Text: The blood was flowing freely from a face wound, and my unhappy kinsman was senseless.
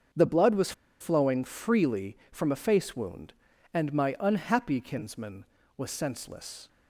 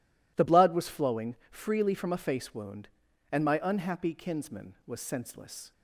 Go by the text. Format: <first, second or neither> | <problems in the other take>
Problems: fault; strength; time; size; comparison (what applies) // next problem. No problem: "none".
second | starts louder than the rest; until 1.4 s; 6.5 dB // pauses between "was" and "flowing"; slight; at 0.7 s; 0.28 s long